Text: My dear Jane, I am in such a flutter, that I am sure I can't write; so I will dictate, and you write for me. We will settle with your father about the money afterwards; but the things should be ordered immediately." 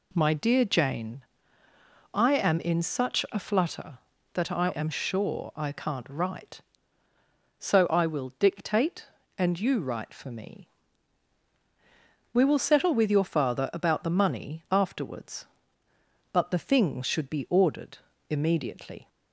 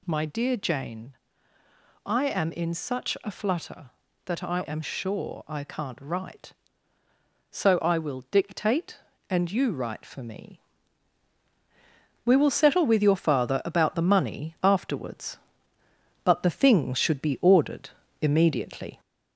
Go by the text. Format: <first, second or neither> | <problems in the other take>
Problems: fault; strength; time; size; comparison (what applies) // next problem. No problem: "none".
first | gets louder; slight; throughout; 2.5 dB // pauses between "ordered" and "immediately"; slight; at 17.8 s; 0.32 s long; slight in the first